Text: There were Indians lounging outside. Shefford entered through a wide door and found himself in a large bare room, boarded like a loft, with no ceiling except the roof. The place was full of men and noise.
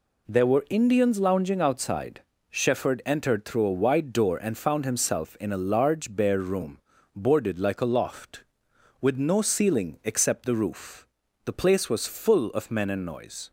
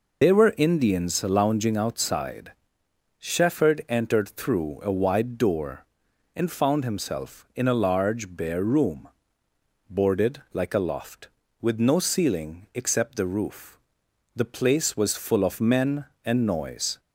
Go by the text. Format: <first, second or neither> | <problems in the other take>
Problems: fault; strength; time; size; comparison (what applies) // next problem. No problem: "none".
first | loses the start of "There"; at 0.2 s; 120 ms